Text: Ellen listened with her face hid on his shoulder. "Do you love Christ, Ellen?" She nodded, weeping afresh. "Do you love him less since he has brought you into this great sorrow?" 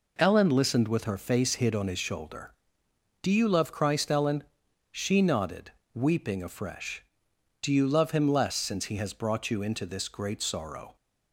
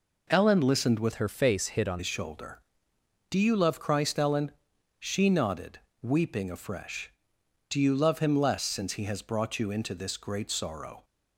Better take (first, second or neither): first